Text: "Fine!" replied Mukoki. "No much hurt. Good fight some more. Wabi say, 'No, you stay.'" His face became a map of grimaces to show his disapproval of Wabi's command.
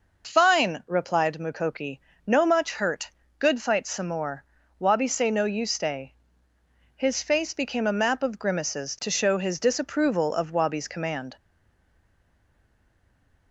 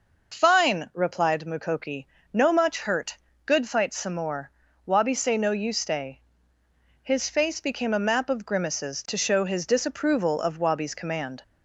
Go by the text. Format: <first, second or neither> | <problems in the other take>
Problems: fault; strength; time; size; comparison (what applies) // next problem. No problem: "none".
second | stays silent after the last word; from 11.3 s on; 2.2 s long